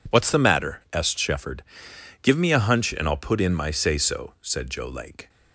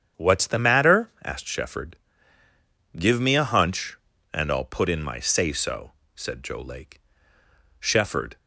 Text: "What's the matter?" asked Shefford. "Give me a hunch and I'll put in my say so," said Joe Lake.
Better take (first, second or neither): first